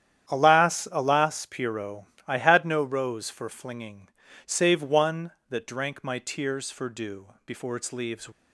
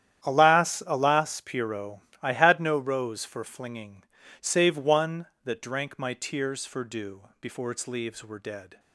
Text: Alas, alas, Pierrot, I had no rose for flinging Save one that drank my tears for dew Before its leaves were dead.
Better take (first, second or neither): second